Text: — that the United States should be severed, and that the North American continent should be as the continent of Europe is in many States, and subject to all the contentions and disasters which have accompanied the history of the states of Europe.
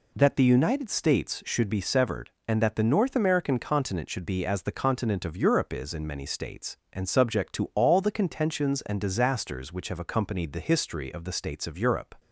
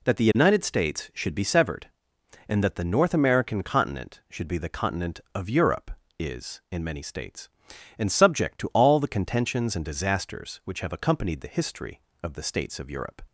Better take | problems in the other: first | skips "as"; at 4.5 s

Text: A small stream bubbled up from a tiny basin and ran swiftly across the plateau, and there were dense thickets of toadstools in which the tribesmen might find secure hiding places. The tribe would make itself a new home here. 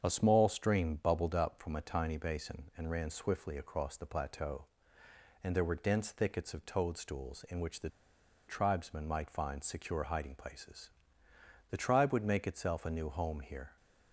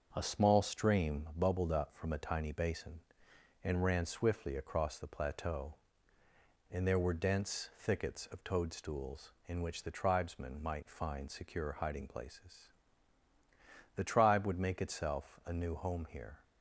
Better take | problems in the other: second | starts louder than the rest; until 1.0 s; 7 dB; also in the second // pauses between "the" and "tribesmen"; noticeable; at 7.8 s; 0.59 s long

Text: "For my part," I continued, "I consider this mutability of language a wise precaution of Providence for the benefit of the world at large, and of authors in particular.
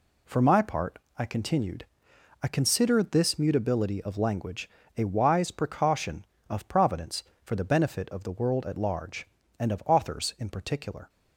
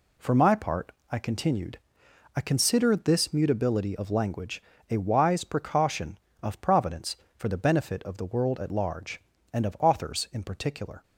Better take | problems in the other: neither | pauses between "language" and "a"; slight; the same in both

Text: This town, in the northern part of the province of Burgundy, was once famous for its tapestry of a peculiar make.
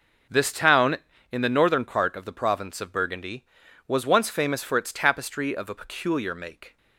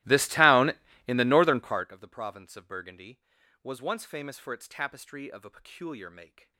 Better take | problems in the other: first | starts louder than the rest; strong; until 1.9 s; 17.5 dB

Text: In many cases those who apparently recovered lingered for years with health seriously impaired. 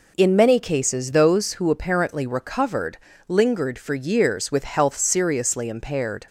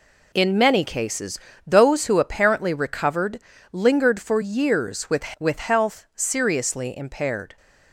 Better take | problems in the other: first | pauses between "cases" and "those"; slight; at 1.3 s; 0.28 s long // pauses between "recovered" and "lingered"; slight; at 3.3 s; 0.32 s long; slight in the first // says "with" twice; at 5.4 s

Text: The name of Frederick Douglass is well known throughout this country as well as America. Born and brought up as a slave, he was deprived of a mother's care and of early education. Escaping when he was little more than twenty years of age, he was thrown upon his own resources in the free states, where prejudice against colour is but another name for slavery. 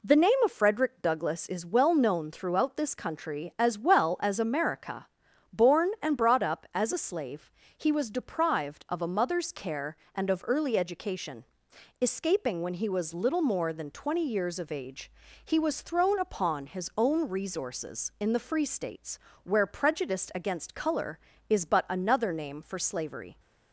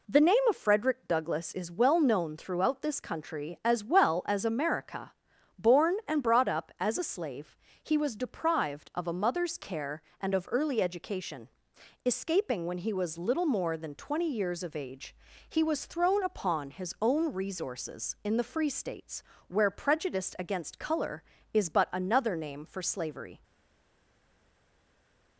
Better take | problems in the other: first | stays silent after the last word; noticeable; from 23.4 s on; 1.9 s long

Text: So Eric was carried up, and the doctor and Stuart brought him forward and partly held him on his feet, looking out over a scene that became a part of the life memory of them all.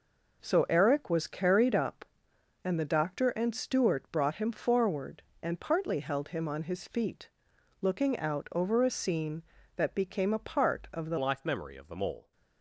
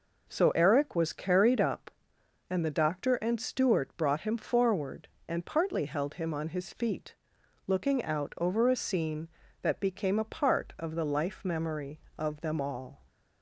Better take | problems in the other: second | changes voice at "life"; from 11.1 s on; 1.2 s long

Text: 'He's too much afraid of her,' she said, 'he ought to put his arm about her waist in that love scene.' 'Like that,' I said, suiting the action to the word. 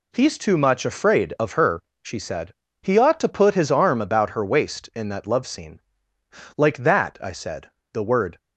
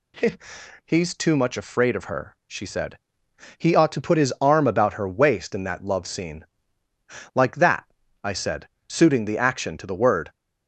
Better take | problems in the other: second | skips "suiting the action to"; at 7.8 s

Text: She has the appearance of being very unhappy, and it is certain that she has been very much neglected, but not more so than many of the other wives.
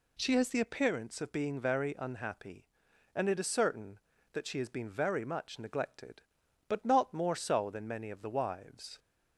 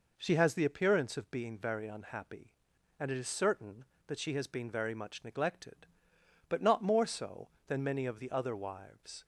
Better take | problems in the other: second | skips "other"; at 8.3 s

